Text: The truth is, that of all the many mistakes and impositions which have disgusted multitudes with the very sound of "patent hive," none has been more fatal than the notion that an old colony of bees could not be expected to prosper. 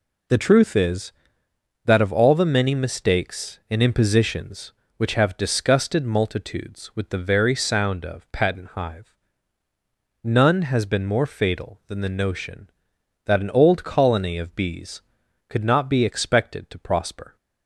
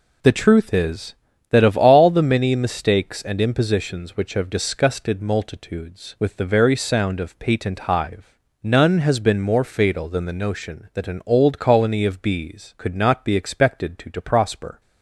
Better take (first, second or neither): first